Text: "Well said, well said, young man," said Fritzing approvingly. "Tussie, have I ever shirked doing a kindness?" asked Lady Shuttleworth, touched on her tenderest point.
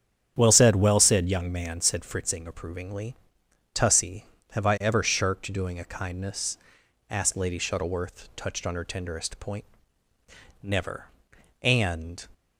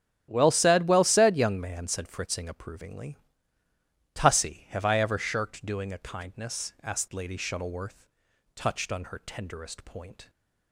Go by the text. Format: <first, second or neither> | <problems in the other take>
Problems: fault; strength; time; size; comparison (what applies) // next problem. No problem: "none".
second | starts louder than the rest; strong; until 1.3 s; 8.5 dB; strong in the second // goes on to say "Never And"; from 10.6 s on; 1.6 s long